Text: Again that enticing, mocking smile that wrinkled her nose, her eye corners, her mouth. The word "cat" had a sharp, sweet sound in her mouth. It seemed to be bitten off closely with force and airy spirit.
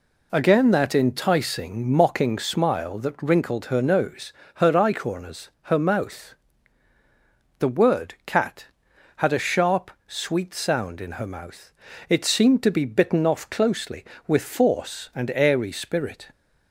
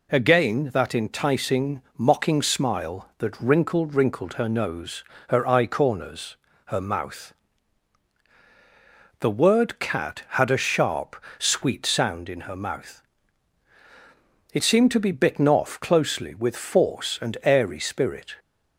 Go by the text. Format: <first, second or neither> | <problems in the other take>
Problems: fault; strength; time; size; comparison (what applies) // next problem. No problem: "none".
first | says "wrinkled" twice; at 3.9 s